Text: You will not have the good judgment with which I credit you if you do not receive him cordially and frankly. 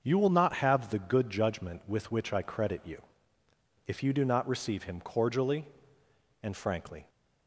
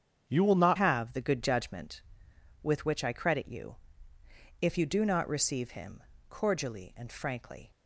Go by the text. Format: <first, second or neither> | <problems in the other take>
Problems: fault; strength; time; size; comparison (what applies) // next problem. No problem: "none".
first | starts louder than the rest; strong; until 1.2 s; 8 dB; also in the first // changes voice at "have"; from 0.7 s on; 7.0 s long // pauses between "you" and "if"; noticeable; at 3.7 s; 0.84 s long; noticeable in the first // pauses between "him" and "cordially"; slight; at 6.0 s; 0.26 s long